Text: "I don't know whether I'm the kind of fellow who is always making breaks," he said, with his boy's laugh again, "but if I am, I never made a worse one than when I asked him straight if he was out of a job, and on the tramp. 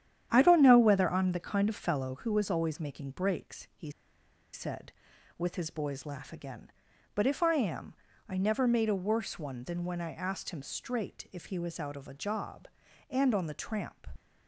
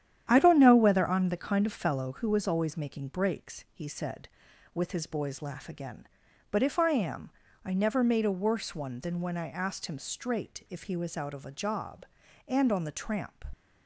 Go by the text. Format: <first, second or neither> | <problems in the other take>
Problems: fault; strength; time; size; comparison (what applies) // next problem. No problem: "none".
second | starts louder than the rest; strong; until 1.3 s; 10 dB; strong in the second // pauses between "he" and "said"; noticeable; at 3.9 s; 0.62 s long